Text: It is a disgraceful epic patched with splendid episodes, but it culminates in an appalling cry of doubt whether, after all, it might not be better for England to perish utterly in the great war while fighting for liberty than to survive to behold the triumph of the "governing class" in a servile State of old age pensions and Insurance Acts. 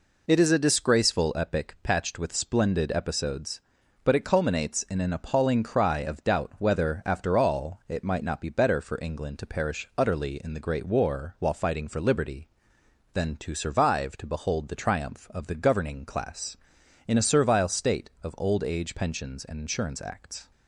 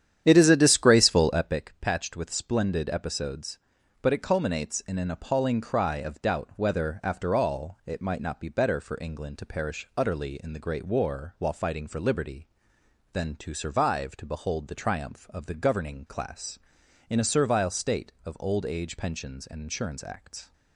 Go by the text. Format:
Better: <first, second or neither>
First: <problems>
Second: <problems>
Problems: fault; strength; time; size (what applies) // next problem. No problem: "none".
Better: first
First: none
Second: starts louder than the rest; strong; until 1.6 s; 10 dB